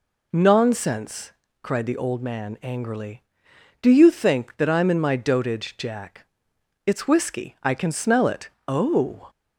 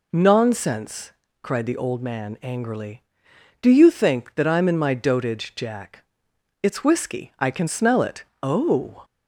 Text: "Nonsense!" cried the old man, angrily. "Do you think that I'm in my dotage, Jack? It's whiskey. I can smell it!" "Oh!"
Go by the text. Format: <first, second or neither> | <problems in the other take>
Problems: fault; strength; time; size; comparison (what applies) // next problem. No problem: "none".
neither | none